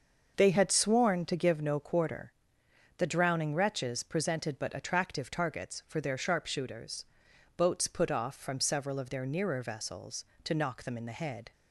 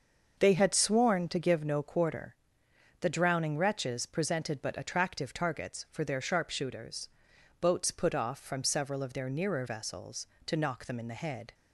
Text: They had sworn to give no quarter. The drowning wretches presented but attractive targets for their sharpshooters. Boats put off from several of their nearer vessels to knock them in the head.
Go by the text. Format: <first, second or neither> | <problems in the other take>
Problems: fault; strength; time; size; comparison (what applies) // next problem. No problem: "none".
neither | starts louder than the rest; the same in both